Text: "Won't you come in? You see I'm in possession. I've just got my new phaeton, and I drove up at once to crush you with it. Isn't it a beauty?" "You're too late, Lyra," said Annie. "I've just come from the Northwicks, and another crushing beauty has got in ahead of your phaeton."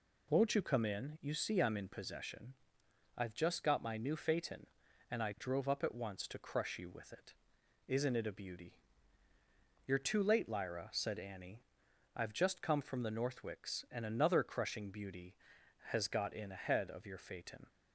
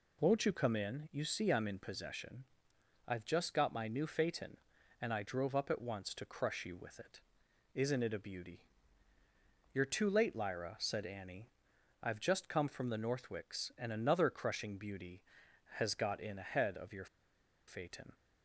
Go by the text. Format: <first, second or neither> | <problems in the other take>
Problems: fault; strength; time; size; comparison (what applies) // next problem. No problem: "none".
first | pauses between "your" and "phaeton"; noticeable; at 17.0 s; 0.62 s long